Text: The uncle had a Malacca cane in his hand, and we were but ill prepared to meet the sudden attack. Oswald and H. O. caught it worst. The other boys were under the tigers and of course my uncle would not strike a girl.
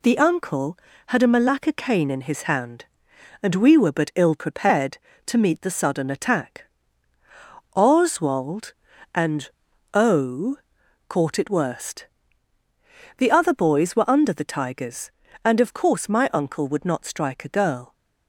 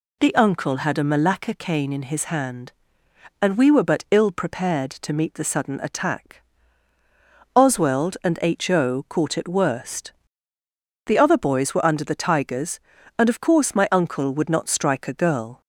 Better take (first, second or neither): second